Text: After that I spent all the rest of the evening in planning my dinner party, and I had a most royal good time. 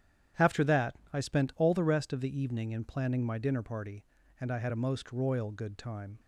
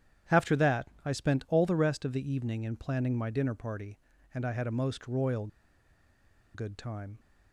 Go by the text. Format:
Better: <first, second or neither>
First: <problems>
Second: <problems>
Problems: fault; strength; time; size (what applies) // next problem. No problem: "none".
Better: first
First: starts louder than the rest; strong; until 1.5 s; 10 dB // pauses between "that" and "I"; slight; at 0.9 s; 0.18 s long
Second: starts louder than the rest; strong; until 1.5 s; 10 dB // pauses between "that" and "I"; slight; at 0.8 s; 0.18 s long // pauses between "royal" and "good"; at 5.4 s; 1.0 s long